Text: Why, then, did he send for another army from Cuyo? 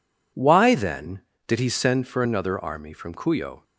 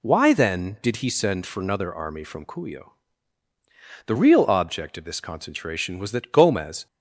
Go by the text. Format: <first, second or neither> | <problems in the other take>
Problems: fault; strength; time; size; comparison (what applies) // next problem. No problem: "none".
first | goes on to say "The real object of this concentration was that Gomez"; strong; from 4.0 s on; 2.8 s long